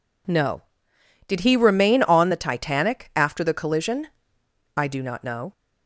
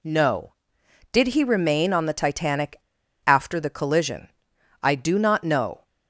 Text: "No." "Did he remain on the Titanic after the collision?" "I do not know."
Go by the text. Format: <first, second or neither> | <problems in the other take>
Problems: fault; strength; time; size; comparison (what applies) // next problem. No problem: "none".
first | pauses between "Titanic" and "after"; noticeable; at 2.8 s; 0.46 s long